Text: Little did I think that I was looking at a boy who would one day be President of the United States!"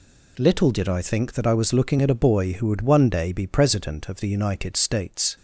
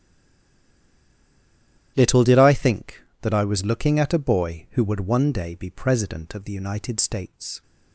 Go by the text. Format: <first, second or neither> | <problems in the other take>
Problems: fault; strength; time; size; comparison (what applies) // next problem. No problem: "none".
first | stays silent before the first word; noticeable; until 1.9 s; 1.9 s long // starts louder than the rest; strong; until 2.9 s; 12 dB